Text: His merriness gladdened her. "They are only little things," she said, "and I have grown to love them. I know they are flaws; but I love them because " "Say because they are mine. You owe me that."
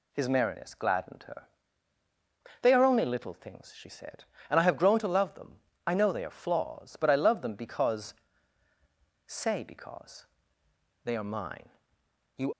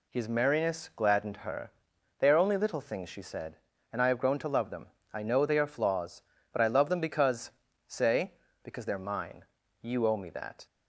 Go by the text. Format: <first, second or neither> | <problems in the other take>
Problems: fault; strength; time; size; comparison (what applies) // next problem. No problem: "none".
second | pauses between "because" and "they"; noticeable; at 10.2 s; 0.78 s long // stops before "owe me that"; at 12.5 s